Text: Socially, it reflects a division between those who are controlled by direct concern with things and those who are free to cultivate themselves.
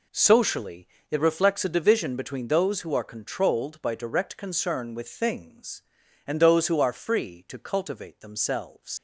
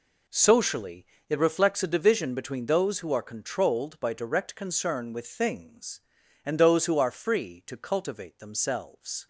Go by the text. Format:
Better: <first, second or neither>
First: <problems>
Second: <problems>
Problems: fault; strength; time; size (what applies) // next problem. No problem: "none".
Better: second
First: leaves "themselves" unfinished; at 8.9 s; 110 ms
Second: none